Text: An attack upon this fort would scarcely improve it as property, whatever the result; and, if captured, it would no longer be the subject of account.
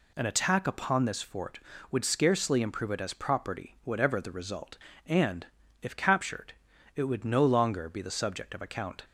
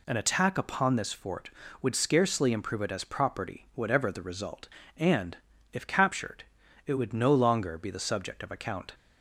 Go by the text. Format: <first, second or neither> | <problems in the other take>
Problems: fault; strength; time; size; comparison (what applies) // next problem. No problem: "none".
neither | none